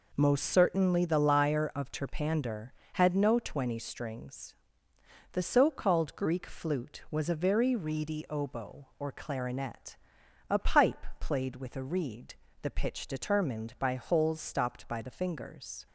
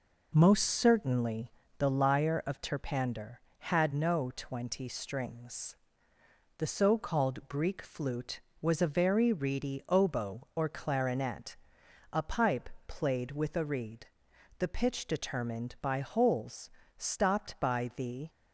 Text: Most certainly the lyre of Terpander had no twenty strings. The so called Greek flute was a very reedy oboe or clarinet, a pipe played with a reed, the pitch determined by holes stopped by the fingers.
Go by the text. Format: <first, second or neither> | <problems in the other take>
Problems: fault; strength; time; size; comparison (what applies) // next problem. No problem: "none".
first | pauses between "certainly" and "the"; slight; at 1.5 s; 0.26 s long // pauses between "pipe" and "played"; slight; at 12.6 s; 0.18 s long // pauses between "holes" and "stopped"; slight; at 16.6 s; 0.28 s long // stops before "fingers"; at 18.2 s